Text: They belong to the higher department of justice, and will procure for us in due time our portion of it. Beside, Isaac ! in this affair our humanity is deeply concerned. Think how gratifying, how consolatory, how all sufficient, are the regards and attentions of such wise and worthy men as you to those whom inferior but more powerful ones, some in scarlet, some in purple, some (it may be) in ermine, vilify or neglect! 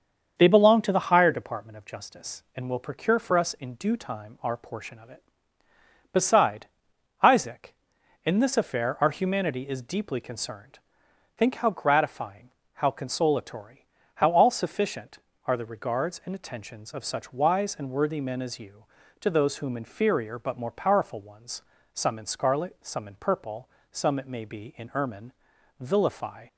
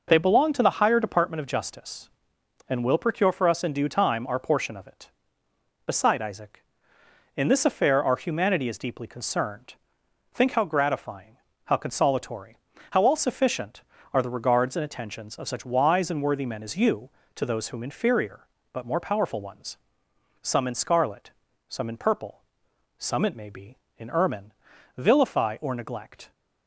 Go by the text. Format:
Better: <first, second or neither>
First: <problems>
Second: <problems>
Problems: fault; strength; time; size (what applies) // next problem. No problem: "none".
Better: second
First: starts louder than the rest; until 1.3 s; 7 dB // stops before "or neglect"; at 26.4 s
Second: none